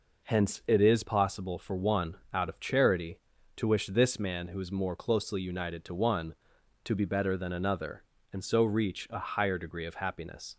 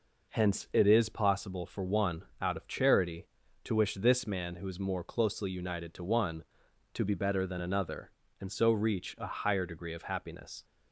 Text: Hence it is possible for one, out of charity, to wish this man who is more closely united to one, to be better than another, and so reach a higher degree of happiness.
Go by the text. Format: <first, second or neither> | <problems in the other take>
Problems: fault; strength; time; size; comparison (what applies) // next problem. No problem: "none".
neither | none